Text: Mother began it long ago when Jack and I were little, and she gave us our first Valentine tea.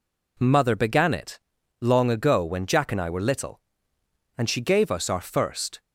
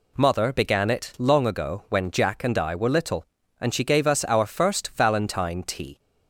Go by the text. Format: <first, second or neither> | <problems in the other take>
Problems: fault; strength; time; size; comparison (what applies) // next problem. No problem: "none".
second | pauses between "it" and "long"; at 1.3 s; 0.40 s long // stops before "Valentine tea"; at 5.7 s